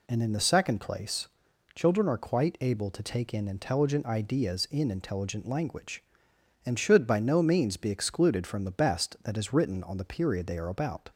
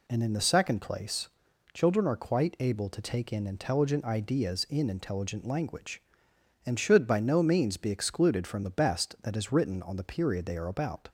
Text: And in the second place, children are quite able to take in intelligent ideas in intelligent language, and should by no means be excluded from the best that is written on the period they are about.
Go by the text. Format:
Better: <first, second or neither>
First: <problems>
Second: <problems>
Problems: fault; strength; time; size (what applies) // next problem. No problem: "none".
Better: neither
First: none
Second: none